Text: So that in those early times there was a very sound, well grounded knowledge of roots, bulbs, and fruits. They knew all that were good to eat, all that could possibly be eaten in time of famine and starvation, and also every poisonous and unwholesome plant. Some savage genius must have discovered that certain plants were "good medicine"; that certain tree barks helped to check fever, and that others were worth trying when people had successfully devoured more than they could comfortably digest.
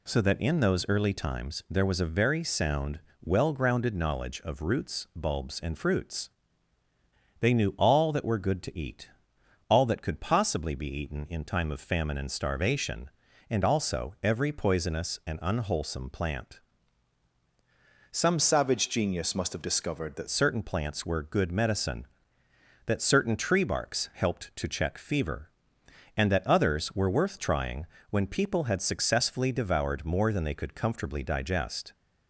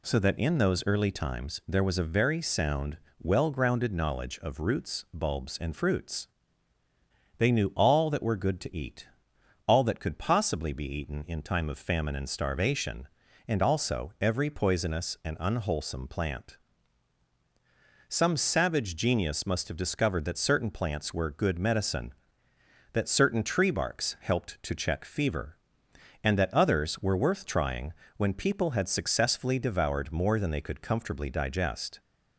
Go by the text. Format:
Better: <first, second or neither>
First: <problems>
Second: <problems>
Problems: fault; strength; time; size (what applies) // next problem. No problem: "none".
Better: second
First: changes voice from "savage" to "that"; from 18.3 to 20.2 s; 1.9 s long // pauses between "trying" and "when"; slight; at 27.8 s; 0.24 s long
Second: pauses between "trying" and "when"; slight; at 27.9 s; 0.24 s long